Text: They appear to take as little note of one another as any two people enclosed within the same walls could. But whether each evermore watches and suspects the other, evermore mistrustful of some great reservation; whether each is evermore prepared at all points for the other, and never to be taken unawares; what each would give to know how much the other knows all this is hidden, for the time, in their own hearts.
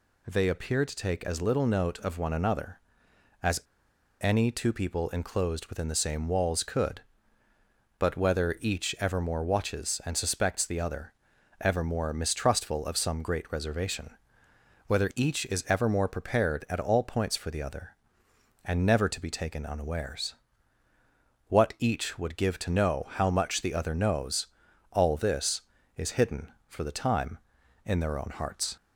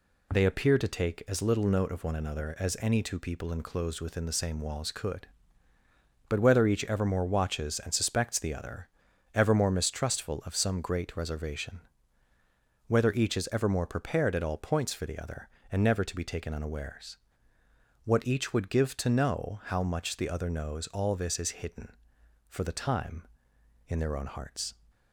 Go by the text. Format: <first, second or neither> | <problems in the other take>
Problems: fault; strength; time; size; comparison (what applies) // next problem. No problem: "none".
second | pauses between "as" and "any"; noticeable; at 3.5 s; 0.61 s long // pauses between "knows" and "all"; at 24.4 s; 0.44 s long